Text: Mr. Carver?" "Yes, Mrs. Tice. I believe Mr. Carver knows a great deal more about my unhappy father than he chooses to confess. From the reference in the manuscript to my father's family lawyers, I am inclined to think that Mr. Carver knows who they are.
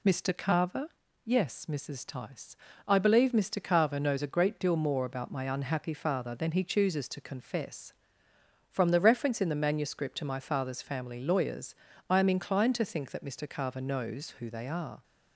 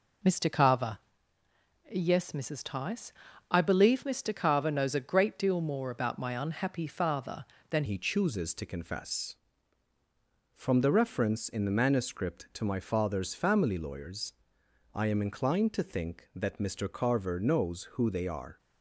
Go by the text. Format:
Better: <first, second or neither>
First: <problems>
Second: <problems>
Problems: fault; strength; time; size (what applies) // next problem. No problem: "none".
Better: first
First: none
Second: changes voice at "he"; from 7.8 s on; 10.7 s long